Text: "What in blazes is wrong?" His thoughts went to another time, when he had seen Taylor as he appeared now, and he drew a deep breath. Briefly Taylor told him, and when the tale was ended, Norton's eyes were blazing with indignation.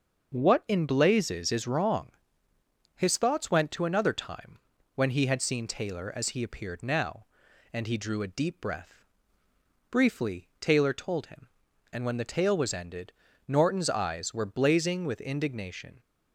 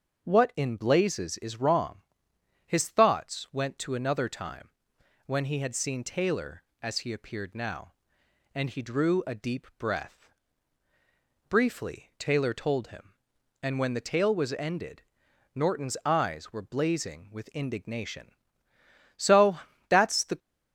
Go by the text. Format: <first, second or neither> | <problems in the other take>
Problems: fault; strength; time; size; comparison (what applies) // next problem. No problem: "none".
first | starts louder than the rest; until 1.2 s; 6.5 dB; noticeable in the first // goes on to say "So that's the"; noticeable; from 19.1 s on; 1.2 s long